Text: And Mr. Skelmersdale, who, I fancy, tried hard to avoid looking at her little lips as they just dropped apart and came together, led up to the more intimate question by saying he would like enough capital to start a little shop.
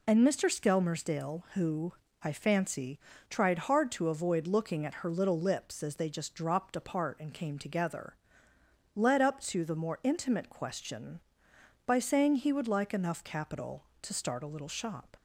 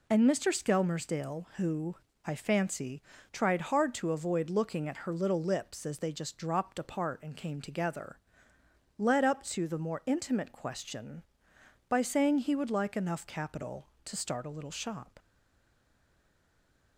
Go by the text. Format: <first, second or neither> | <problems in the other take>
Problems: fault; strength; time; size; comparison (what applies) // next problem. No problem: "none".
first | stays silent after the last word; noticeable; from 15.1 s on; 1.8 s long